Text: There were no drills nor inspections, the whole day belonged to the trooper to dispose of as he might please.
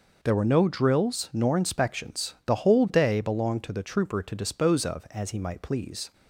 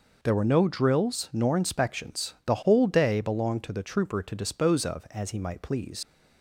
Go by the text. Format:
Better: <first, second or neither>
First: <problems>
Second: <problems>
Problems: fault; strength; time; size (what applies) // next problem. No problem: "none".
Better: first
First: none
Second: leaves "please" unfinished; at 6.0 s; 95 ms